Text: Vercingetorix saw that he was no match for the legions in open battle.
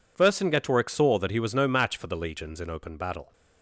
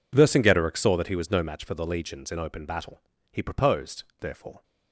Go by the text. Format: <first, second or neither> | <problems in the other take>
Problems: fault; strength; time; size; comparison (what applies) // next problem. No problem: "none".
first | goes on to say "He proposed therefore"; from 3.3 s on; 1.3 s long